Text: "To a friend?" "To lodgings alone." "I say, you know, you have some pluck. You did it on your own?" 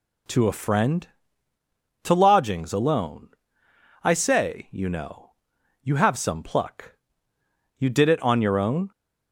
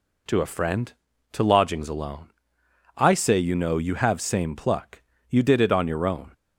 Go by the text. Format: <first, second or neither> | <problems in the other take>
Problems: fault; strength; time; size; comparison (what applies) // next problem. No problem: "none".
first | says "same" for "some"; at 4.2 s